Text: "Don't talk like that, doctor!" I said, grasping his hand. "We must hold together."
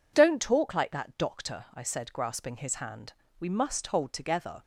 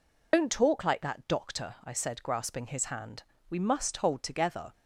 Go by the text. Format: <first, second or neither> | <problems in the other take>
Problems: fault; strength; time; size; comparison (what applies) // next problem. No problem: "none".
first | loses the start of "Don't"; at 0.3 s; 90 ms